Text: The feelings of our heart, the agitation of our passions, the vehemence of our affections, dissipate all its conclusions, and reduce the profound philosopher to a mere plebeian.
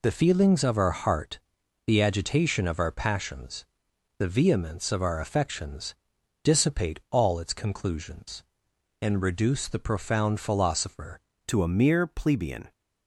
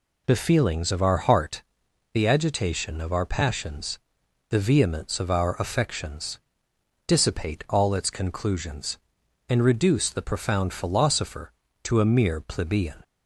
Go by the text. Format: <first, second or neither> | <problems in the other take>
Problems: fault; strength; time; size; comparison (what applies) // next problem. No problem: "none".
second | changes voice at "to"; from 11.4 s on; 1.3 s long